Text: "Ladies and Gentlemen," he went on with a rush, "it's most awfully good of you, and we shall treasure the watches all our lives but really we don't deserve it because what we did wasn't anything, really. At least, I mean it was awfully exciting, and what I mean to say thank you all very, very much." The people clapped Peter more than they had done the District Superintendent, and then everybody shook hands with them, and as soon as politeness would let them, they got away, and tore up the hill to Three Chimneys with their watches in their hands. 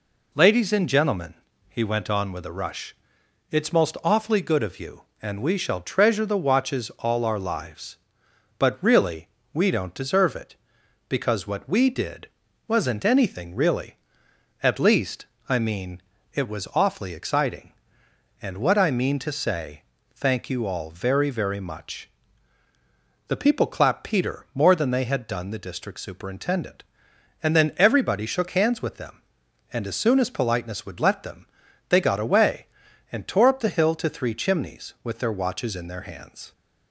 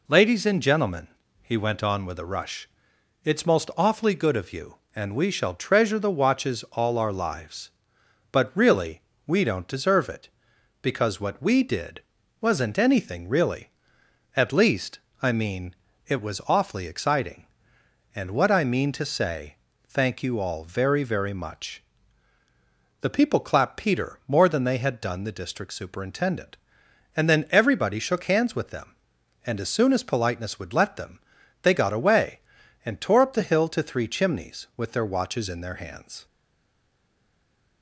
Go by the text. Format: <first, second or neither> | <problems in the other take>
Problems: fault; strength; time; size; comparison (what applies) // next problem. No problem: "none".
first | pauses between "really" and "we"; slight; at 9.0 s; 0.24 s long; slight in the first // pauses between "did" and "wasn't"; at 12.0 s; 0.40 s long; also in the first // pauses between "mean" and "it"; slight; at 15.7 s; 0.32 s long; slight in the first // pauses between "say" and "thank"; slight; at 19.5 s; 0.32 s long; slight in the first // stays silent after the last word; noticeable; from 36.2 s on; 1.6 s long